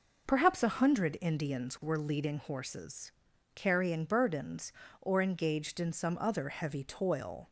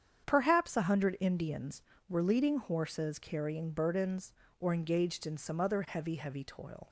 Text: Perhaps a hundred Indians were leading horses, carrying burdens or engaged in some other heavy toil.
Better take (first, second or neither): first